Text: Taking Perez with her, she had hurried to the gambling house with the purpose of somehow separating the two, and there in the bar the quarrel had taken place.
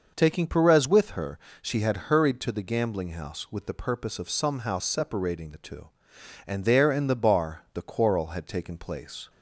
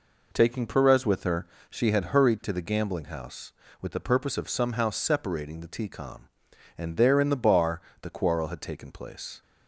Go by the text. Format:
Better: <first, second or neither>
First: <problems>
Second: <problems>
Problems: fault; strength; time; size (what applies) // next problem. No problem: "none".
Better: first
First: none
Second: says "tcom" for "two"; at 5.8 s // pauses between "bar" and "the"; slight; at 7.8 s; 0.20 s long